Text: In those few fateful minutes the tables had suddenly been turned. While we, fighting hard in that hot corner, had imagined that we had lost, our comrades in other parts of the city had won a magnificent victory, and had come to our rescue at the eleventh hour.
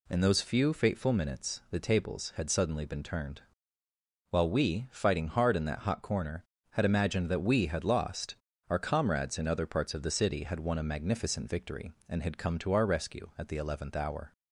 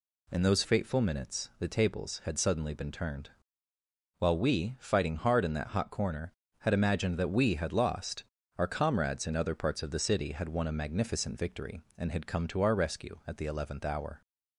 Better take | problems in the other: first | skips "few"; at 0.6 s

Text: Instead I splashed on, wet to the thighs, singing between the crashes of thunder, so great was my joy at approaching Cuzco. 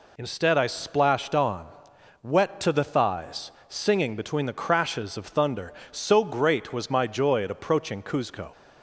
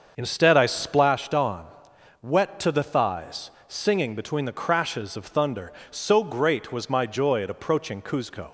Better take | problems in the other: first | starts louder than the rest; until 1.1 s; 6.5 dB

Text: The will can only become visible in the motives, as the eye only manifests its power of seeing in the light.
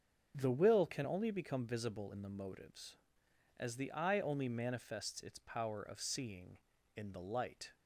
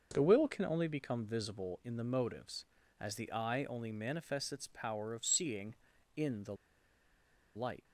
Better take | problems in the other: first | starts louder than the rest; until 1.1 s; 6 dB; also in the first // pauses between "the" and "light"; at 6.5 s; 1.0 s long

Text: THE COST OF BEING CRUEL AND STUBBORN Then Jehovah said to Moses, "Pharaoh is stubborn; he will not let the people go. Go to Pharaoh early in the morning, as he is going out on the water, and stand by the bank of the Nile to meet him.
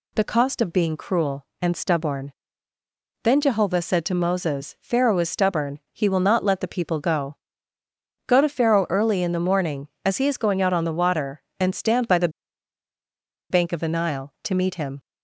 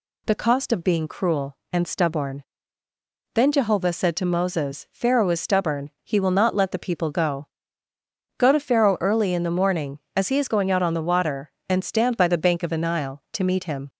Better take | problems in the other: second | pauses between "STUBBORN" and "Then"; noticeable; at 2.3 s; 0.90 s long; noticeable in the second // pauses between "the" and "bank"; at 12.2 s; 1.2 s long

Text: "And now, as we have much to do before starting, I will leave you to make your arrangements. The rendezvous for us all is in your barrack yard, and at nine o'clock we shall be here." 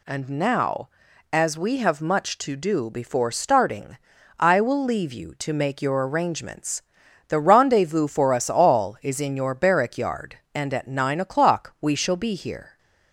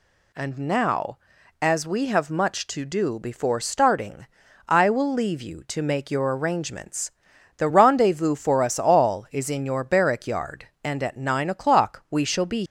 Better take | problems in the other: first | stops before "here"; at 12.6 s

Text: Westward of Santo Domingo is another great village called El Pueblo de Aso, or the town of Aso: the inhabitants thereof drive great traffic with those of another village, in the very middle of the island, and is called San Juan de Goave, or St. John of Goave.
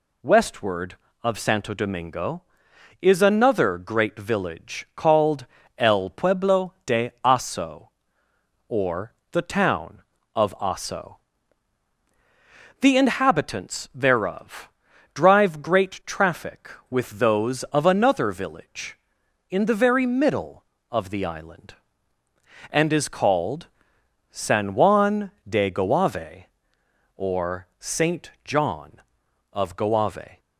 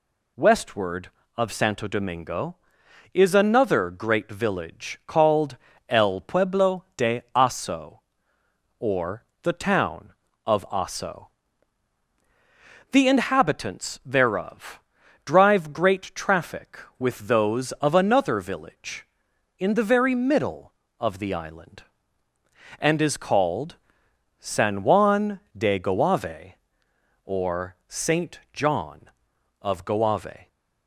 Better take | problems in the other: neither | pauses between "called" and "El"; slight; the same in both // pauses between "or" and "the"; slight; the same in both // pauses between "thereof" and "drive"; the same in both // pauses between "called" and "San"; noticeable; the same in both // pauses between "Juan" and "de"; slight; the same in both

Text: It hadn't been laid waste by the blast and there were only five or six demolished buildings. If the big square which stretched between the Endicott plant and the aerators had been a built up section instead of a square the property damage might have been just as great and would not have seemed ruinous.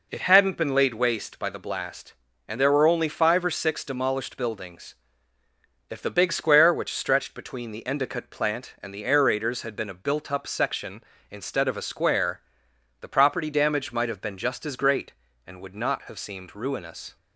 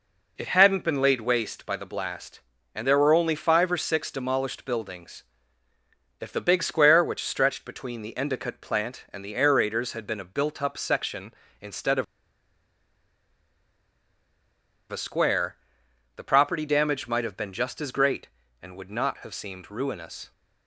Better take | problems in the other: first | pauses between "of" and "a"; strong; at 12.0 s; 2.8 s long // pauses between "square" and "the"; noticeable; at 15.5 s; 0.60 s long; noticeable in the first

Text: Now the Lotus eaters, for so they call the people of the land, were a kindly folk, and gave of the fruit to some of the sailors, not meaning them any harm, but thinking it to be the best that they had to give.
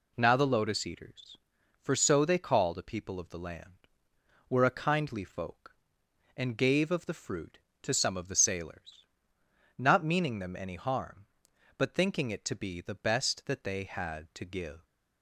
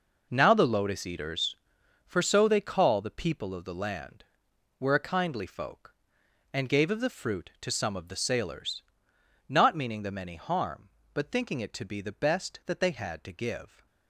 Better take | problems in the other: first | gets quieter; strong; throughout; 11 dB

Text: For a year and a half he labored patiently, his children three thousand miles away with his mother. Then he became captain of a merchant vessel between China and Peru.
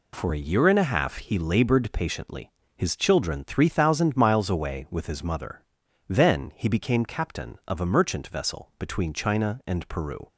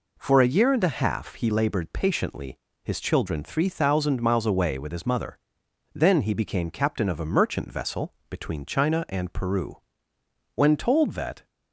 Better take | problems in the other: first | pauses between "vessel" and "between"; slight; at 8.1 s; 0.18 s long // goes on to say "When told that"; noticeable; from 10.5 s on; 0.92 s long

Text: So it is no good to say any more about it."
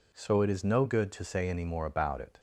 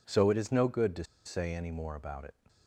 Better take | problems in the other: first | pauses between "to" and "say"; slight; at 1.0 s; 0.21 s long

